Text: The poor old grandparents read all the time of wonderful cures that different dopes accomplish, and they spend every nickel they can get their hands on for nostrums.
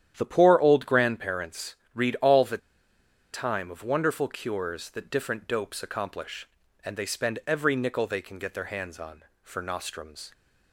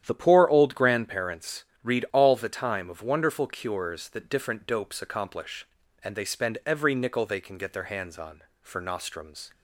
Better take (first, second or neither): second